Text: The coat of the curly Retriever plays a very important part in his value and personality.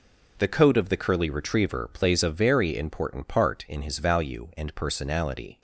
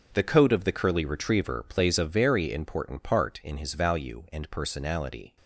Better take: first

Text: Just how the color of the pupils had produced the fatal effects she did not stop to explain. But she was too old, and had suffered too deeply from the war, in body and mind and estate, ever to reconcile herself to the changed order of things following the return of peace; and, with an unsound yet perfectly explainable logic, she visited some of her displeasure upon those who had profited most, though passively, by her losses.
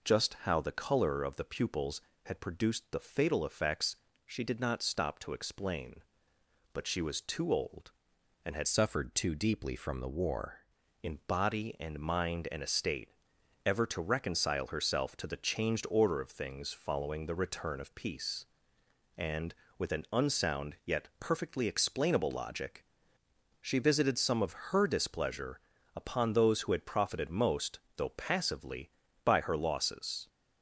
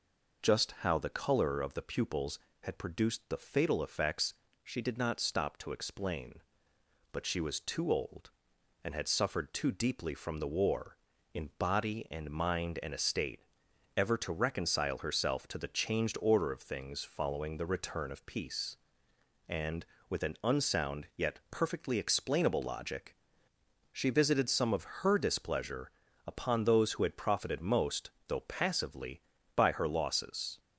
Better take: second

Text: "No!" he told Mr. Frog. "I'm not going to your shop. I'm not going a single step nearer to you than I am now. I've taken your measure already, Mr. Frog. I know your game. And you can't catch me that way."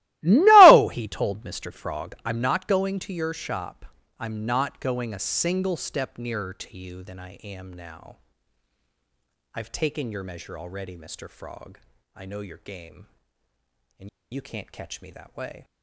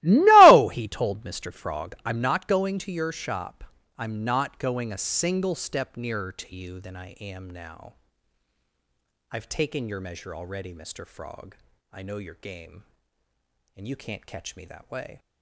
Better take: second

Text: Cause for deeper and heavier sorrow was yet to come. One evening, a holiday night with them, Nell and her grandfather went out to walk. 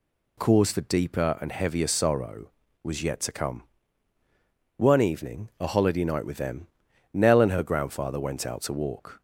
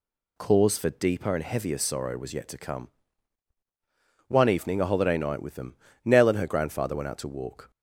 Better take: neither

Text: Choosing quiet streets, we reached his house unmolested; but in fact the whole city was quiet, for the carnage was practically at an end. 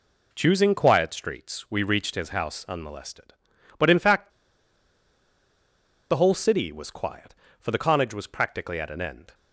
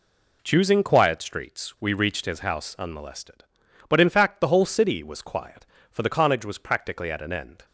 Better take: second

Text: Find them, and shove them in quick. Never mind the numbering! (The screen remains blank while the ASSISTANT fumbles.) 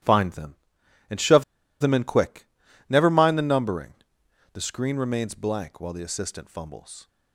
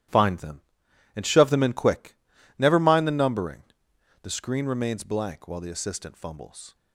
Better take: second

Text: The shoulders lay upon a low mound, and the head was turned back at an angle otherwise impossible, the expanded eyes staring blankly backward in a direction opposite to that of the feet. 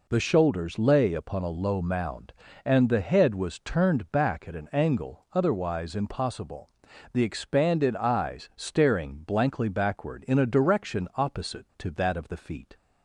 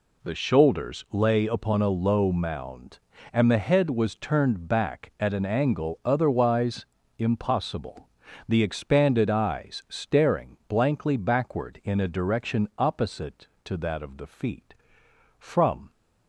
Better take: first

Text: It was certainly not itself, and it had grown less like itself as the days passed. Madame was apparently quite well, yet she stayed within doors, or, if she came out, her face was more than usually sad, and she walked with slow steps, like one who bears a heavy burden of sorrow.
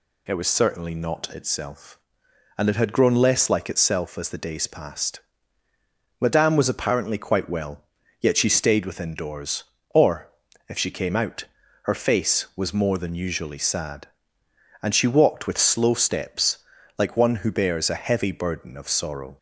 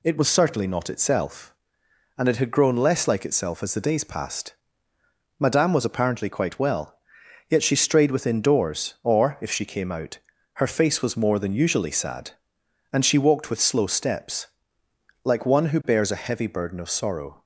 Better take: first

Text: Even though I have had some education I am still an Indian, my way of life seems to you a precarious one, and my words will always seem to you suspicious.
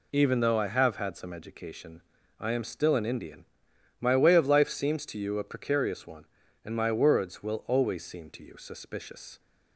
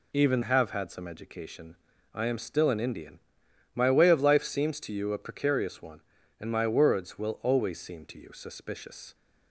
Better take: first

